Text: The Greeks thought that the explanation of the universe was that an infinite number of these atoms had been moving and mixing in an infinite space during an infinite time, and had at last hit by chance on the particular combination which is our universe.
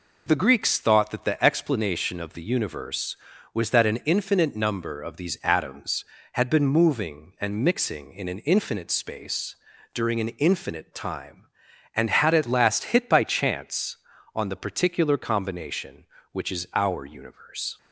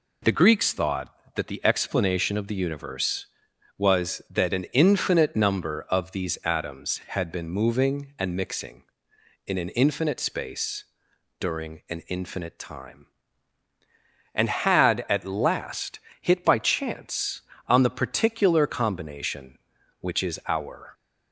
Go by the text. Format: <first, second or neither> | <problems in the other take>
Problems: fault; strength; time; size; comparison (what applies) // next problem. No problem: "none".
first | pauses between "space" and "during"; noticeable; at 10.8 s; 0.54 s long; also in the first // pauses between "last" and "hit"; slight; at 15.9 s; 0.22 s long // stops before "universe"; at 20.9 s